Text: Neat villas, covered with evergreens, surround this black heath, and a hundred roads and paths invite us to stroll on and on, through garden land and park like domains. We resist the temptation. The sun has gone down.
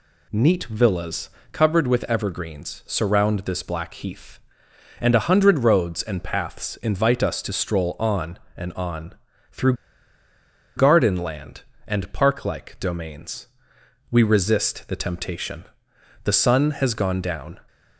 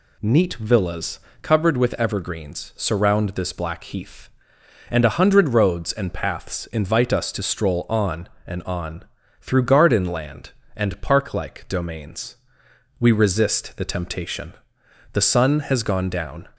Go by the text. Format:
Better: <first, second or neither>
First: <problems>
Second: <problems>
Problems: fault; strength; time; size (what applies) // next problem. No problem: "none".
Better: second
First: pauses between "through" and "garden"; at 9.7 s; 1.0 s long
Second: none